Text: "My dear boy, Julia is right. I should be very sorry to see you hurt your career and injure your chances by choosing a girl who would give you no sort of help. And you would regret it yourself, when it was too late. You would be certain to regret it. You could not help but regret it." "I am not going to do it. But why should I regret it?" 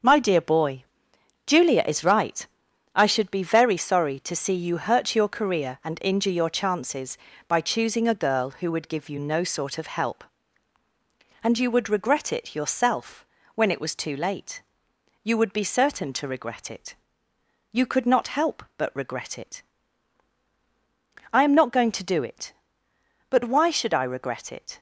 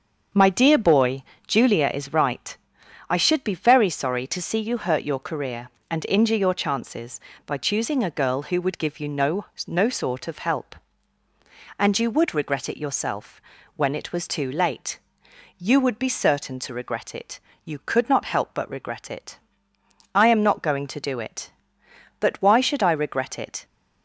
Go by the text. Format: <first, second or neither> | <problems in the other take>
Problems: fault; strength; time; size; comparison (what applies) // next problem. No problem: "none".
first | starts louder than the rest; until 1.5 s; 7 dB; also in the first // says "no" twice; at 9.6 s